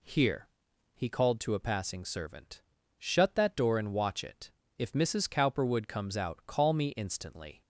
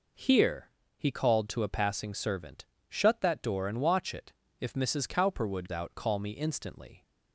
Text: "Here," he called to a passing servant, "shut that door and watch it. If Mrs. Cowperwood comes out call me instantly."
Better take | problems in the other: first | skips "comes"; at 5.6 s

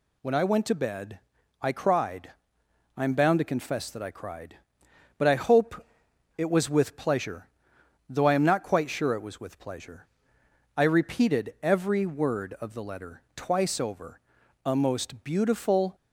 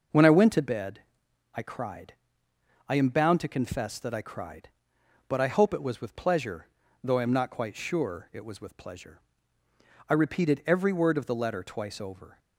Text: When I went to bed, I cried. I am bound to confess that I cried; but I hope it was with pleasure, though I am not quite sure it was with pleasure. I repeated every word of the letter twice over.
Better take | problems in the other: second | pauses between "hope" and "it"; noticeable; at 5.8 s; 0.52 s long // pauses between "letter" and "twice"; slight; at 13.2 s; 0.16 s long // goes on to say "A most beautiful"; noticeable; from 14.6 s on; 1.3 s long

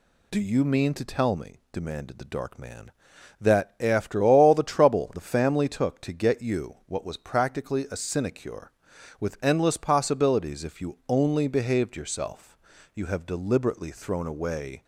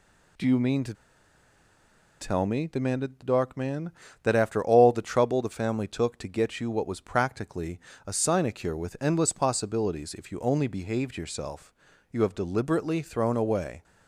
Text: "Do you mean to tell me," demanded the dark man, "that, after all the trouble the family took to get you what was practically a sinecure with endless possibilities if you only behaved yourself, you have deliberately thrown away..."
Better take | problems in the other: first | pauses between "to" and "tell"; strong; at 0.9 s; 1.2 s long // pauses between "practically" and "a"; slight; at 7.8 s; 0.26 s long

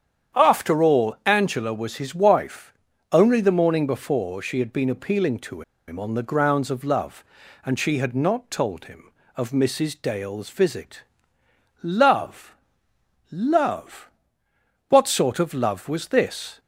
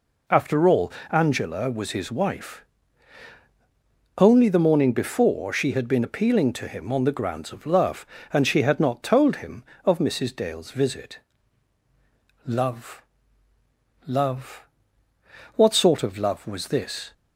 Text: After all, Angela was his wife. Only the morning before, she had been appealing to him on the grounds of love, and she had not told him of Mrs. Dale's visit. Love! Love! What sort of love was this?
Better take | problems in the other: second | starts louder than the rest; strong; until 1.4 s; 9 dB // pauses between "to" and "him"; slight; at 5.6 s; 0.26 s long

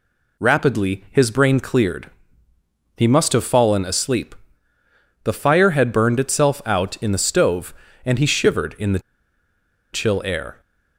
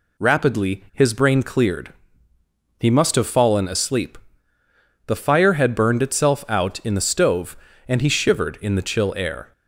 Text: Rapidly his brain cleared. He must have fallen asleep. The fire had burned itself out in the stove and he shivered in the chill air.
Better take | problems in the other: second | pauses between "the" and "chill"; noticeable; at 8.9 s; 0.93 s long

